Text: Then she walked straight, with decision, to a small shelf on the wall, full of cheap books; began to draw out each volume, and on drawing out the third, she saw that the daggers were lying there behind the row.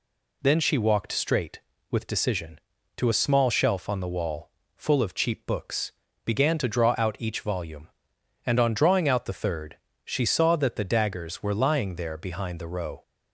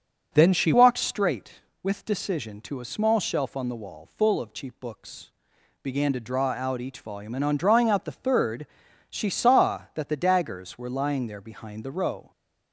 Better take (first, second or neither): first